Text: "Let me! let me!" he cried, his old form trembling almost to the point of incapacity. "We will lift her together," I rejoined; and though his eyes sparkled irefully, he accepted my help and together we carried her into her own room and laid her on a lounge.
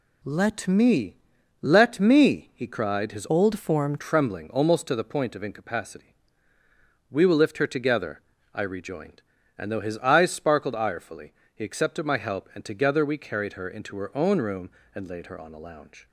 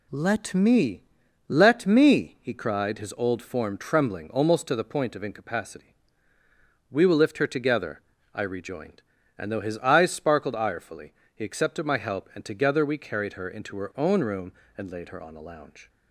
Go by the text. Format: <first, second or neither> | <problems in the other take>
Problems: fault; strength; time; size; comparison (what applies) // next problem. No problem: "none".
second | changes voice from "old" to "form"; from 3.2 to 3.9 s; 0.7 s long